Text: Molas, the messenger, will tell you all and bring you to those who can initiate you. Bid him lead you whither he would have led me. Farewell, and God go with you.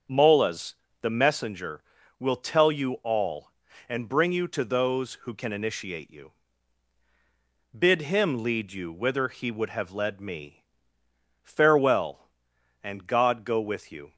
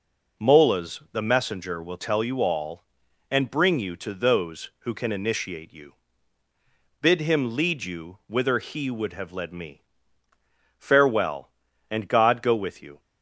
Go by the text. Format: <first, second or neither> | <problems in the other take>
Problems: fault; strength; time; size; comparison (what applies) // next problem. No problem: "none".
second | starts louder than the rest; until 1.4 s; 7 dB